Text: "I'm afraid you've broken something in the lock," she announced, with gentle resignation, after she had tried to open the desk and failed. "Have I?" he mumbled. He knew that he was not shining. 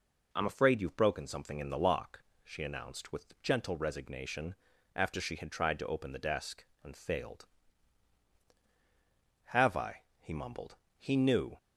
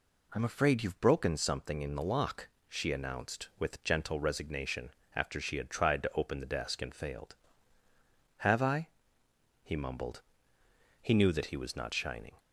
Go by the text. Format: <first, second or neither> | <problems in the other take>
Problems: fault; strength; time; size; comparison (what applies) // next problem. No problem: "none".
second | stops before "that he was not shining"; at 11.5 s